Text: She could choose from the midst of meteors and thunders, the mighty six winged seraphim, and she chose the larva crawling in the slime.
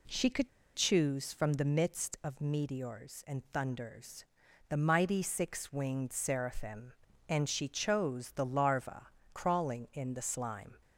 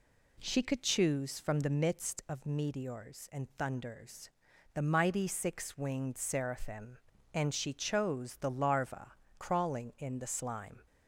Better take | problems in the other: second | pauses between "could" and "choose"; slight; at 0.4 s; 0.27 s long // pauses between "larva" and "crawling"; slight; at 9.0 s; 0.24 s long; slight in the second

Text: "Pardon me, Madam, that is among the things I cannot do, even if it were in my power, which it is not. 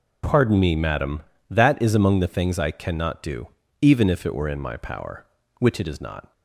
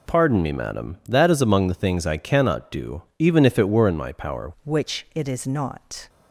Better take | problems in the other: first | changes voice at "which"; from 4.6 s on; 1.4 s long

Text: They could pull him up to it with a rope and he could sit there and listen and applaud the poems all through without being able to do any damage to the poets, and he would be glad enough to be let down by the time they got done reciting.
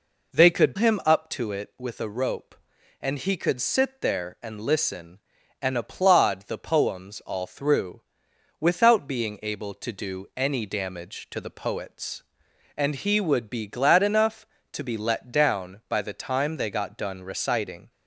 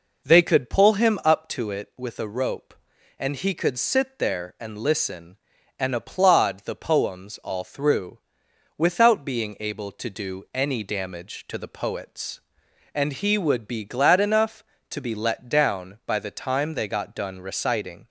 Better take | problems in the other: second | skips "pull"; at 0.7 s // pauses between "through" and "without"; noticeable; at 7.9 s; 0.60 s long; noticeable in the second

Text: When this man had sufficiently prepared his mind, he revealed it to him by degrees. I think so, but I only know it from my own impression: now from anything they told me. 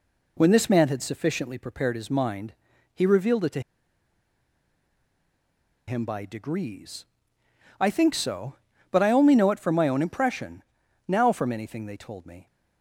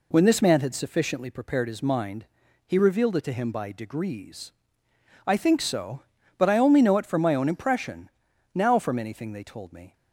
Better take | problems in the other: second | pauses between "to" and "him"; strong; at 3.5 s; 2.2 s long

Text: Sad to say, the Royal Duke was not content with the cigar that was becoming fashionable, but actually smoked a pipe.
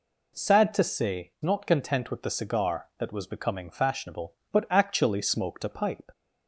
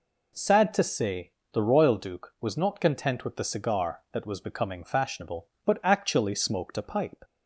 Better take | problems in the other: second | skips "the Royal Duke was"; at 1.3 s

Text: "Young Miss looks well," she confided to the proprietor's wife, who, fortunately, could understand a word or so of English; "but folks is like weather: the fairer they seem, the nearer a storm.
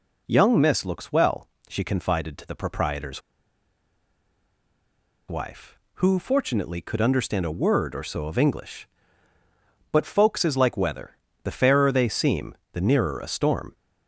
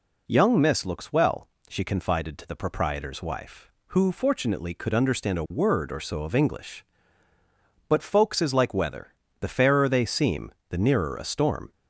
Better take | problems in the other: second | pauses between "proprietor's" and "wife"; strong; at 3.2 s; 2.0 s long

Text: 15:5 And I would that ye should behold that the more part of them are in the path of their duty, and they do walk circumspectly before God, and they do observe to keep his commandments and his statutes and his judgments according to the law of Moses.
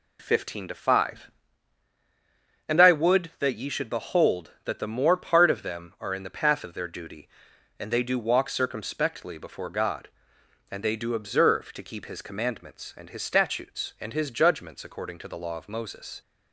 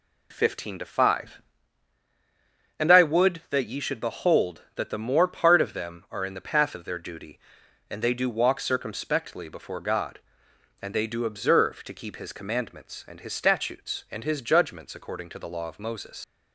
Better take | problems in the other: first | leaves "Moses" unfinished; at 16.2 s; 75 ms

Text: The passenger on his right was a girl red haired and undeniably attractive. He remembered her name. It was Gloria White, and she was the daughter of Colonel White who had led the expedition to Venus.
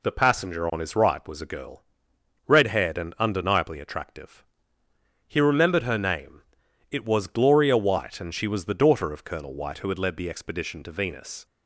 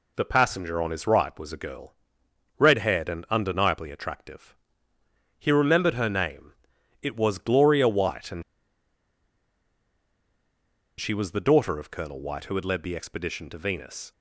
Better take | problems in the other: first | pauses between "girl" and "red"; noticeable; at 1.9 s; 0.64 s long; noticeable in the first // pauses between "and" and "she"; strong; at 8.4 s; 2.5 s long

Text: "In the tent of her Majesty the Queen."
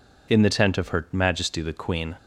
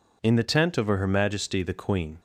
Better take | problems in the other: neither | none

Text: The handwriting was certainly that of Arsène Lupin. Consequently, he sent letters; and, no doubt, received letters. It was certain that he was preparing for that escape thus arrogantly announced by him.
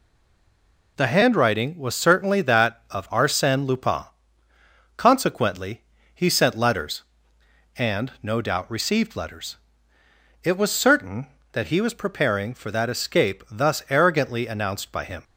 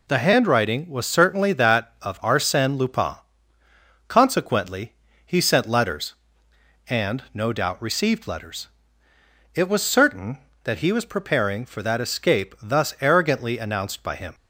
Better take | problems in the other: second | stays silent before the first word; slight; until 0.9 s; 0.9 s long

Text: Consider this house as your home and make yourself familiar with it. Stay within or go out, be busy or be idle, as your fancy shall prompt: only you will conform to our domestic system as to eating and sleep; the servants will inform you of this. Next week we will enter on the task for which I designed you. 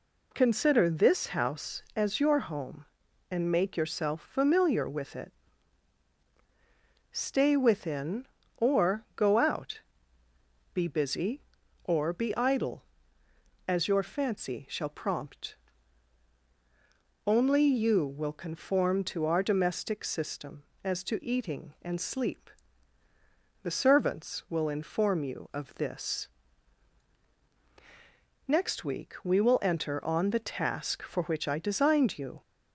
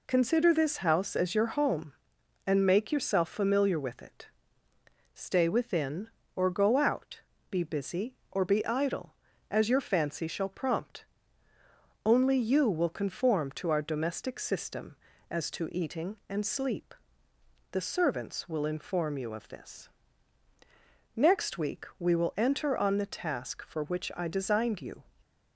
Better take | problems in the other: neither | none

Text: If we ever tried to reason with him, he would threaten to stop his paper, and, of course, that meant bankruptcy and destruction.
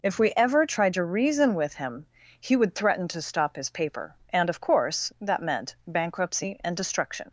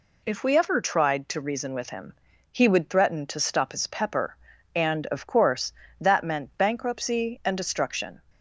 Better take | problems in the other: first | says "pepper" for "paper"; at 3.8 s

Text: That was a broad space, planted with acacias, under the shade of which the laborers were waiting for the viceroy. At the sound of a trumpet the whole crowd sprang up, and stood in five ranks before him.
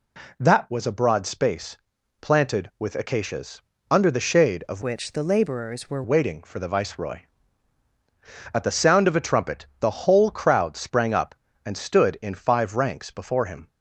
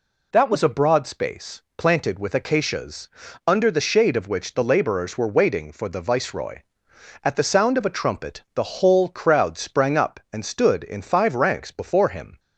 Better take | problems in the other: second | changes voice from "which" to "were"; from 4.8 to 6.0 s; 1.2 s long // pauses between "trumpet" and "the"; slight; at 9.6 s; 0.16 s long

